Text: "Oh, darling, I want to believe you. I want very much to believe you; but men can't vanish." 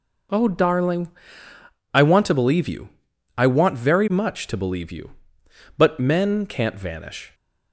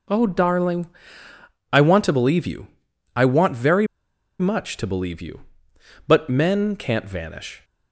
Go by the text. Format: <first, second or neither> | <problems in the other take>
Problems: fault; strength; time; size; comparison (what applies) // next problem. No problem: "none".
first | pauses between "very" and "much"; noticeable; at 3.8 s; 0.53 s long